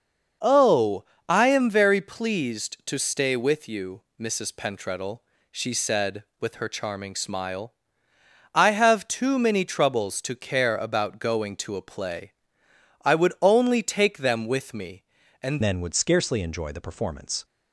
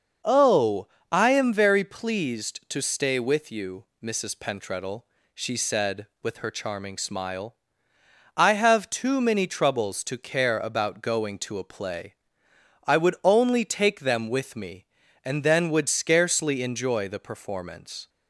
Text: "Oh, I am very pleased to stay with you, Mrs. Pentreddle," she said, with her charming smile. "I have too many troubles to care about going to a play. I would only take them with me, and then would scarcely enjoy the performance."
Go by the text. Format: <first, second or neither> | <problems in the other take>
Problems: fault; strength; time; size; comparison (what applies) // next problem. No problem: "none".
second | starts louder than the rest; noticeable; until 1.6 s; 6 dB; noticeable in the second // changes voice at "then"; from 15.6 s on; 1.8 s long